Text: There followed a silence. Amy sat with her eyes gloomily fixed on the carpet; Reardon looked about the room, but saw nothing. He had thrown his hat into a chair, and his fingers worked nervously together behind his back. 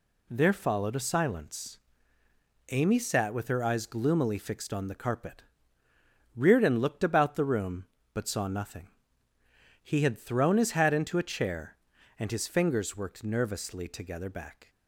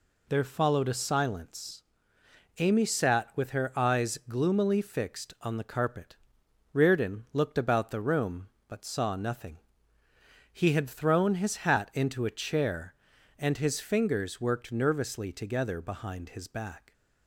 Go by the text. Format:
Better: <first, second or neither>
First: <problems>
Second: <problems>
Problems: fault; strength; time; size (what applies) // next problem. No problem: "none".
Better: second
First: skips "behind his"; at 14.2 s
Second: none